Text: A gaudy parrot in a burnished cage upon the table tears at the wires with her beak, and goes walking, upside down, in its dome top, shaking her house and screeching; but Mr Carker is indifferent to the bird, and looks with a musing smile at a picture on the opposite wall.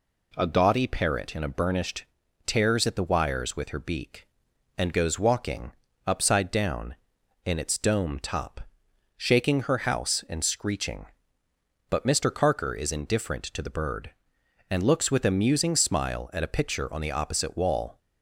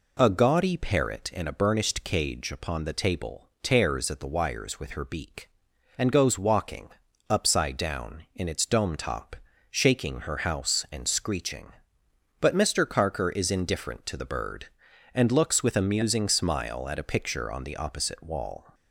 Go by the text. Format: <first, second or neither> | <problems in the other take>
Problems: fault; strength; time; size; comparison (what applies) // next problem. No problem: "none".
second | skips "cage upon the table"; at 2.2 s